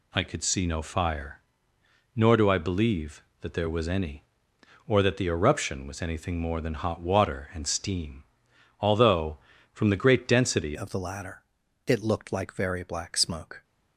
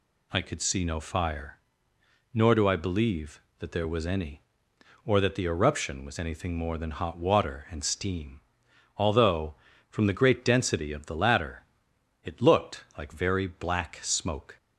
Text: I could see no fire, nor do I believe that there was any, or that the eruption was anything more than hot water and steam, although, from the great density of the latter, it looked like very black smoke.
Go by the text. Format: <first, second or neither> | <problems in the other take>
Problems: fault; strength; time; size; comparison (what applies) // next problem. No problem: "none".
second | changes voice at "of"; from 10.7 s on; 2.9 s long